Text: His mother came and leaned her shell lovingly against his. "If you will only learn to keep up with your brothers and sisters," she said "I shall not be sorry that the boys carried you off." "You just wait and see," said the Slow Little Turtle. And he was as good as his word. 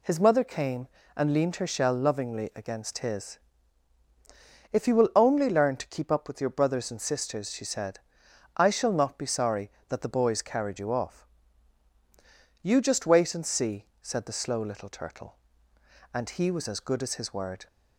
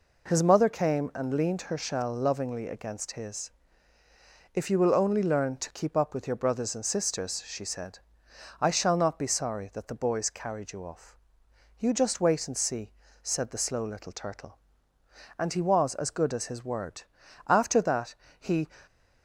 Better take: first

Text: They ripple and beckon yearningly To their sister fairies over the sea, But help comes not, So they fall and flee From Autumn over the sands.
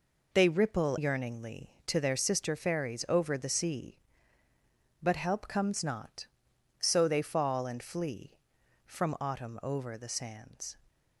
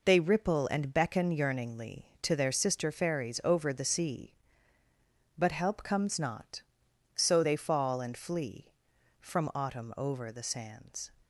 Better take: second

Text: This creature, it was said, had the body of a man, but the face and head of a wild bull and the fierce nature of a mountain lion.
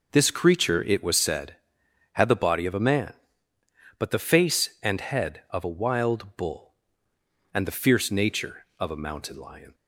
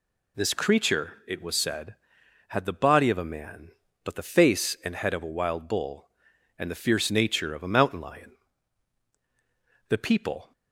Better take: first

